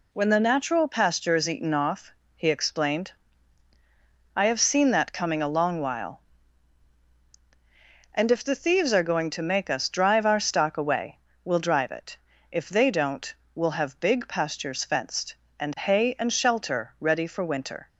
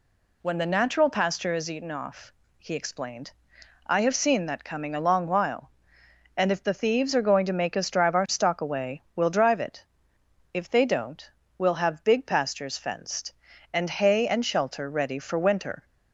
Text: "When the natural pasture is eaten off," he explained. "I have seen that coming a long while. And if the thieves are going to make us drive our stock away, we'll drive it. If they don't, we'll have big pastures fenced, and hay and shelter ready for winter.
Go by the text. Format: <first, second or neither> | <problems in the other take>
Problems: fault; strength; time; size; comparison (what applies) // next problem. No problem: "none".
neither | none